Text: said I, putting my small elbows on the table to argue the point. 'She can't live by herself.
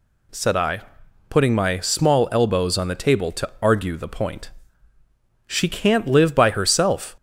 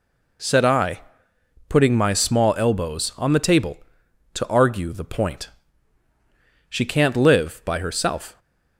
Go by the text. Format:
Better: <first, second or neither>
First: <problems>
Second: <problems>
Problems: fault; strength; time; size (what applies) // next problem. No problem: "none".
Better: neither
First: none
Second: none